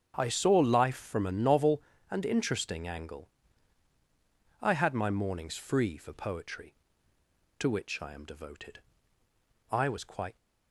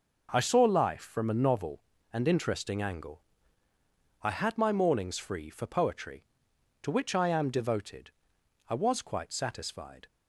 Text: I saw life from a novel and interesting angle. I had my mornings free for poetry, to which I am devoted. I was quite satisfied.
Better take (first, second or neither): second